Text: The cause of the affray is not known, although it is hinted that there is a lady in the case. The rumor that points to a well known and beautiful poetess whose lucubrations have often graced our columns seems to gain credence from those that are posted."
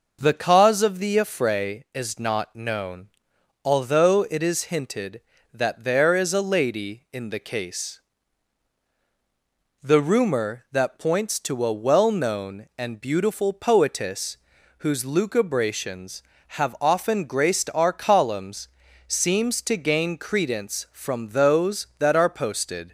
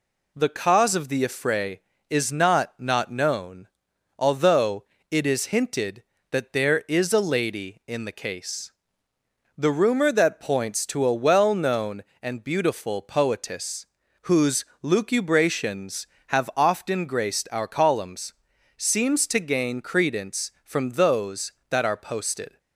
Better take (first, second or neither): first